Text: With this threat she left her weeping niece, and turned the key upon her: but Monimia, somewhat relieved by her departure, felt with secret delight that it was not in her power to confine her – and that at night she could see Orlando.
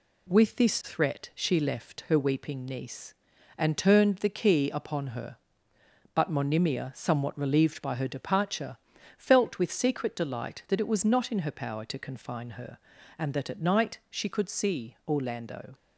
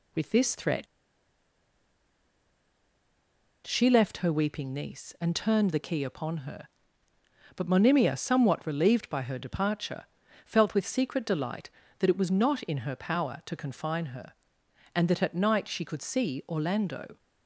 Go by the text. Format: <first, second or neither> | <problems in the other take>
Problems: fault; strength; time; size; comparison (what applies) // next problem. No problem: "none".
first | pauses between "threat" and "she"; strong; at 0.8 s; 2.8 s long